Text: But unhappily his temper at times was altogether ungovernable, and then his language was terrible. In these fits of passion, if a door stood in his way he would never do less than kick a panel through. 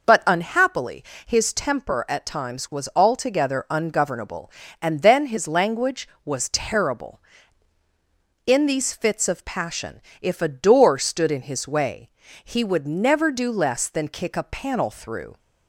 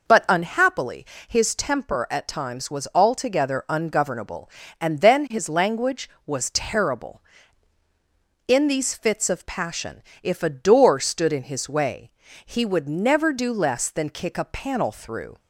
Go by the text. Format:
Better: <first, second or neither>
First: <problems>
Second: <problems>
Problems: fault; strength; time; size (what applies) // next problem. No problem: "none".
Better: neither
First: pauses between "unhappily" and "his"; slight; at 1.0 s; 0.22 s long // pauses between "way" and "he"; slight; at 12.0 s; 0.34 s long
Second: pauses between "unhappily" and "his"; slight; at 1.0 s; 0.22 s long // pauses between "way" and "he"; slight; at 12.1 s; 0.34 s long